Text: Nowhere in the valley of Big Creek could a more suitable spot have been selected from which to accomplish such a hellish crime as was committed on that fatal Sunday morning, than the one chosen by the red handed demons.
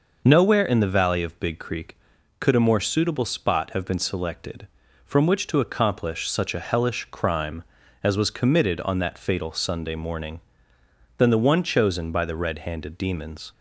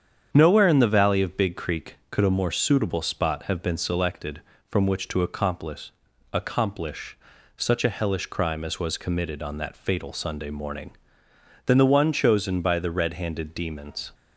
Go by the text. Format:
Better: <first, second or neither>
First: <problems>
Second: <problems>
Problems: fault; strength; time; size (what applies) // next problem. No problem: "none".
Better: first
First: none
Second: starts louder than the rest; strong; until 1.3 s; 8 dB // says "accomplish" twice; at 6.3 s